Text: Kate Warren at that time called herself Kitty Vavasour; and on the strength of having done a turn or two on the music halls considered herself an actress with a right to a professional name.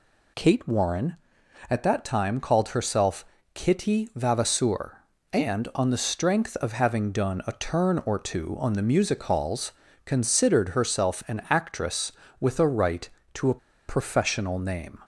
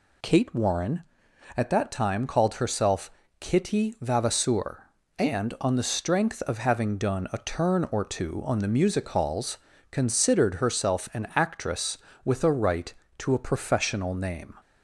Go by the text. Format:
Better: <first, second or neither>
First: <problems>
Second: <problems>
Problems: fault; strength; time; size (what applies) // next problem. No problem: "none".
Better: second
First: pauses between "herself" and "Kitty"; slight; at 3.2 s; 0.30 s long // pauses between "halls" and "considered"; slight; at 9.7 s; 0.34 s long // pauses between "a" and "professional"; slight; at 13.5 s; 0.29 s long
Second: pauses between "herself" and "Kitty"; slight; at 3.0 s; 0.30 s long // pauses between "halls" and "considered"; slight; at 9.5 s; 0.34 s long